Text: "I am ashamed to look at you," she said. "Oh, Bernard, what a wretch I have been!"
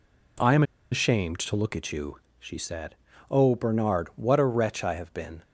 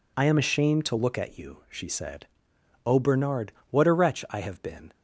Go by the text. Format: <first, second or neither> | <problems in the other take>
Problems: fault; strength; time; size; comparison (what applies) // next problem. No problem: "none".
second | pauses between "am" and "ashamed"; slight; at 0.6 s; 0.29 s long